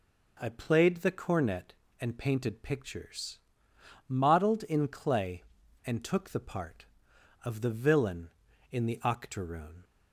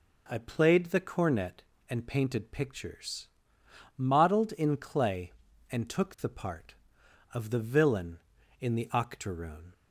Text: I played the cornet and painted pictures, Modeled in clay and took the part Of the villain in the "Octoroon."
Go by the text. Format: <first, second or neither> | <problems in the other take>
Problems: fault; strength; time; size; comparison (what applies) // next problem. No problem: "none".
neither | none